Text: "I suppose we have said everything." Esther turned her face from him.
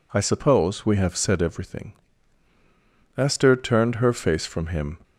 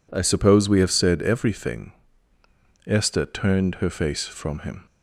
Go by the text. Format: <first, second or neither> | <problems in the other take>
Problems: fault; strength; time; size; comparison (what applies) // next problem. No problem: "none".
neither | none